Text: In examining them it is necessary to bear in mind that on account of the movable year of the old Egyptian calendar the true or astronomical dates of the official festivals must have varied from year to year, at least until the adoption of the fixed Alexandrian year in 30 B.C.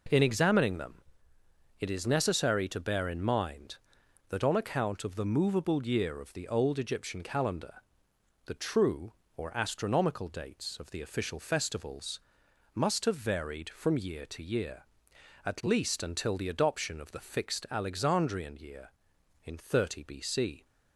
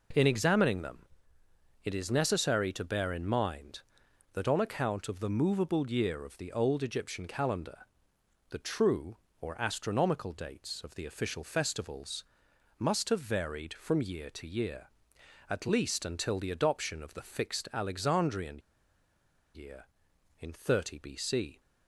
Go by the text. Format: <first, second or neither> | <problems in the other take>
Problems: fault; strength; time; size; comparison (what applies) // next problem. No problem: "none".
first | pauses between "them" and "it"; noticeable; at 0.9 s; 0.86 s long; noticeable in the first // pauses between "calendar" and "the"; noticeable; at 7.7 s; 0.72 s long; noticeable in the first // pauses between "festivals" and "must"; noticeable; at 12.2 s; 0.52 s long; noticeable in the first // pauses between "Alexandrian" and "year"; noticeable; at 18.5 s; 0.95 s long